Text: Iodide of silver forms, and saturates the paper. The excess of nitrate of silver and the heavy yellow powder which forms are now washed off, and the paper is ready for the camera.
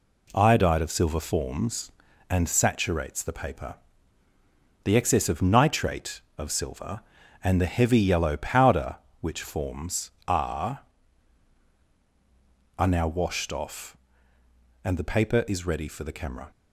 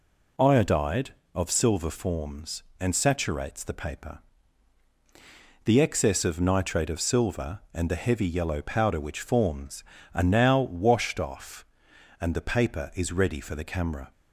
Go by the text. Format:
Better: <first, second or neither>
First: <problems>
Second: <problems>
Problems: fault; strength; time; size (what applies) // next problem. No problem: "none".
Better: second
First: says "are" twice; at 12.7 s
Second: none